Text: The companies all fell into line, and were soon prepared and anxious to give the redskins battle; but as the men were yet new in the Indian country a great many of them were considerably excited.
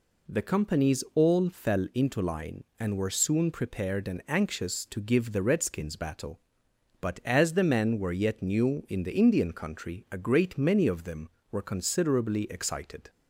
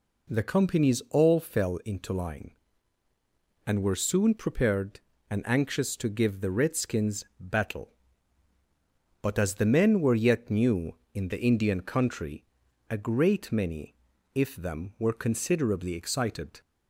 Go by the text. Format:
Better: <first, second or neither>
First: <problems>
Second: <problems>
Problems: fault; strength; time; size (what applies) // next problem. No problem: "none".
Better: first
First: none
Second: pauses between "redskins" and "battle"; slight; at 7.2 s; 0.16 s long // pauses between "country" and "a"; noticeable; at 12.4 s; 0.46 s long // says "if" for "of"; at 14.3 s